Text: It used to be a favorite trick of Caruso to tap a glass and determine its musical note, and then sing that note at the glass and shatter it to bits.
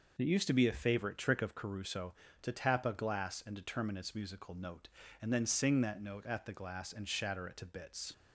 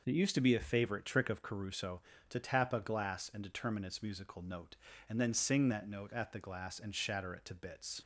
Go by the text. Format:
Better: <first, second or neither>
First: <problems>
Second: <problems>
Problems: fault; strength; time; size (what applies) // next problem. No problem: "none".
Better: neither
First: none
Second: none